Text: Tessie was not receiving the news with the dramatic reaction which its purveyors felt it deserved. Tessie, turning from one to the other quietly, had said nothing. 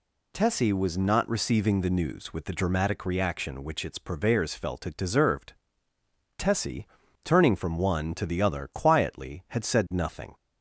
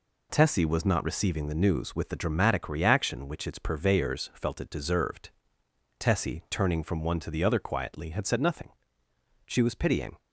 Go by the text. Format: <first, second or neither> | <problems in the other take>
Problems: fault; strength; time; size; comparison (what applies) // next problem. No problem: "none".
first | goes on to say "She was pitying"; noticeable; from 9.4 s on; 0.72 s long